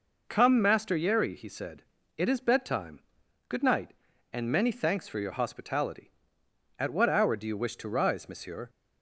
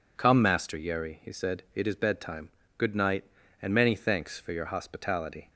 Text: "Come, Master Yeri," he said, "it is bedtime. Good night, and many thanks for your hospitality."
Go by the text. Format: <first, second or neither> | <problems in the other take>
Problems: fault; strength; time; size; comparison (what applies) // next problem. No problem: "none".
second | goes on to say "At what hour do you wish to rise Monsieur"; strong; from 6.7 s on; 1.9 s long